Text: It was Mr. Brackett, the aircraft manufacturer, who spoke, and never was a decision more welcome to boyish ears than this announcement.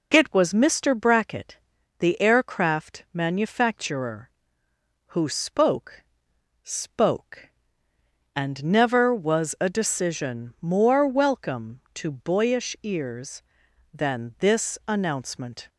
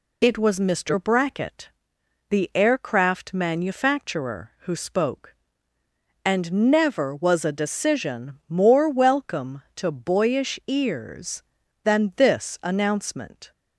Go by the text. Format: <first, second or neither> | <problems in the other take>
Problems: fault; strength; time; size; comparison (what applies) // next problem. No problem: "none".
second | says "spoke" twice; at 6.6 s